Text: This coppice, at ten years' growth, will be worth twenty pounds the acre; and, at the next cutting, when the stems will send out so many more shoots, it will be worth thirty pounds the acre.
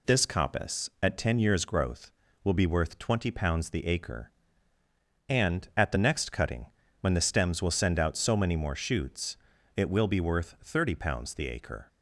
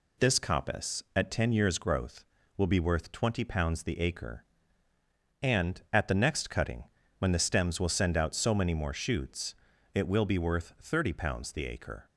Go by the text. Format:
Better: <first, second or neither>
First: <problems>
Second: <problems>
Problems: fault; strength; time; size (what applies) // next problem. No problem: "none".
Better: neither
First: none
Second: none